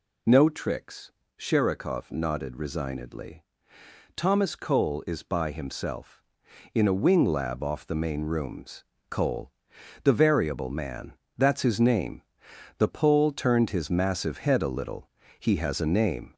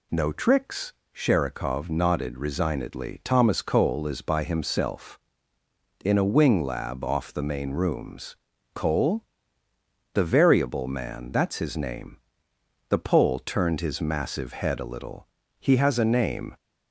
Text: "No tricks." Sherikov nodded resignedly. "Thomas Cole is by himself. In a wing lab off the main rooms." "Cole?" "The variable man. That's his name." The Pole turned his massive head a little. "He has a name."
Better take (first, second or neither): second